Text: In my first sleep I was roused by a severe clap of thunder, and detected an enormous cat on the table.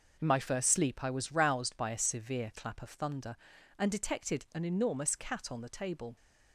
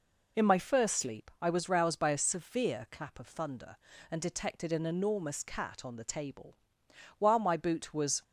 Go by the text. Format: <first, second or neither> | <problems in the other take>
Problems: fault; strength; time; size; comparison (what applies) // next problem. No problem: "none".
first | goes on to say "While my boot was"; noticeable; from 7.1 s on; 1.0 s long